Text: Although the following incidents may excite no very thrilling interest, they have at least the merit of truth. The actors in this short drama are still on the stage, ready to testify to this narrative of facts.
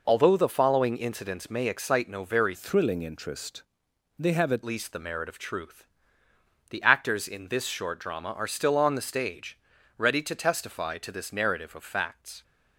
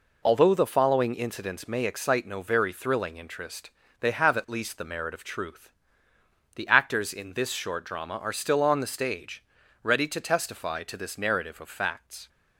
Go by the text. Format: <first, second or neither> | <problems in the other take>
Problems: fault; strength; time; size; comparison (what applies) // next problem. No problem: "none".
second | changes voice from "thrilling" to "at"; from 2.5 to 4.6 s; 2.1 s long